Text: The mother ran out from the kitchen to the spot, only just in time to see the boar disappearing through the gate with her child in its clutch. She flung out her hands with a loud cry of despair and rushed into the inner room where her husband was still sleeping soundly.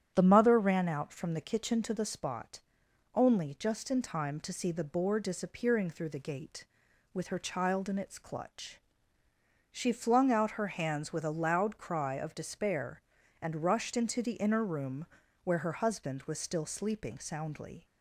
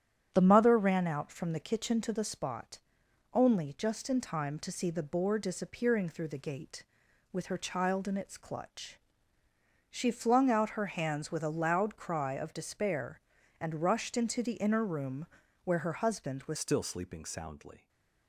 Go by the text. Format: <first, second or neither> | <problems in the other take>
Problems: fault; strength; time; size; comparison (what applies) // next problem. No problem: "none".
first | starts louder than the rest; strong; until 1.3 s; 9.5 dB; strong in the first // pauses between "room" and "where"; at 15.2 s; 0.40 s long; also in the first // changes voice at "still"; from 16.5 s on; 1.3 s long // stays silent after the last word; slight; from 17.7 s on; 0.5 s long